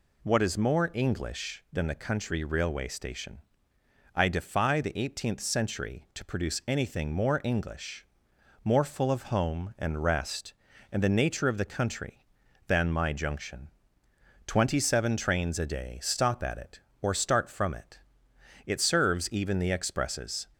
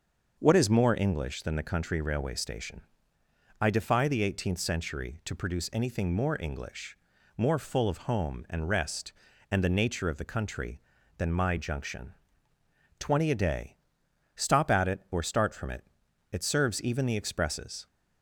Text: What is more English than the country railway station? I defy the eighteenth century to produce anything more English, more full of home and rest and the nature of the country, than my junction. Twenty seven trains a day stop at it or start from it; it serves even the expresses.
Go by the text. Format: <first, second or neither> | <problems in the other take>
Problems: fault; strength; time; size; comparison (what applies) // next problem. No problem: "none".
first | starts louder than the rest; until 1.4 s; 6 dB // skips "seven trains"; at 13.3 s // pauses between "day" and "stop"; noticeable; at 13.7 s; 0.58 s long